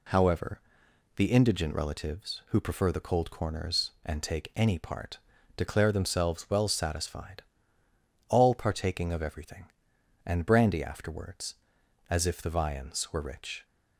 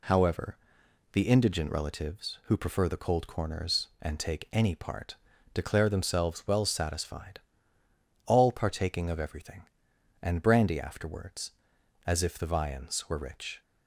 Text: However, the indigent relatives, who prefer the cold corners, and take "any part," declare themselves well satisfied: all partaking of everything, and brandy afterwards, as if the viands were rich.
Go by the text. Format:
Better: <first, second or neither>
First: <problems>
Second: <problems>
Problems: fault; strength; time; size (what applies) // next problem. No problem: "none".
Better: neither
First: none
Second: none